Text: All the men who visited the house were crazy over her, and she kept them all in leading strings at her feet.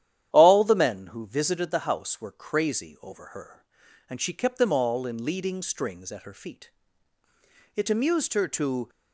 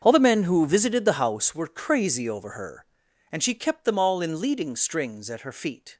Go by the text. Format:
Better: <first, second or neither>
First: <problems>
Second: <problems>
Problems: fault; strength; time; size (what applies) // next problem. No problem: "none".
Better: second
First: starts louder than the rest; strong; until 1.3 s; 11 dB // goes on to say "It amused her to"; noticeable; from 7.7 s on; 1.1 s long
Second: starts louder than the rest; strong; until 1.0 s; 7 dB